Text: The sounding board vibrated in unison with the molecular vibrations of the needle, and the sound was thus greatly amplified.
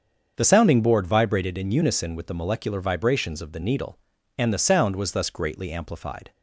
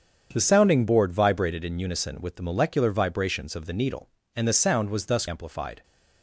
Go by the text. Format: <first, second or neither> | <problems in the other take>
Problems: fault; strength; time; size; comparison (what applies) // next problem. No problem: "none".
first | starts louder than the rest; strong; until 1.3 s; 7.5 dB; also in the first // skips "greatly"; at 5.2 s